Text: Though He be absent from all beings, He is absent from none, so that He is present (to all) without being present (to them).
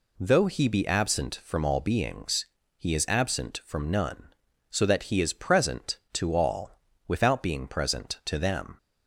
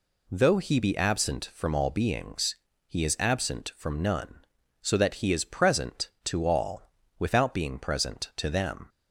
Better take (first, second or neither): neither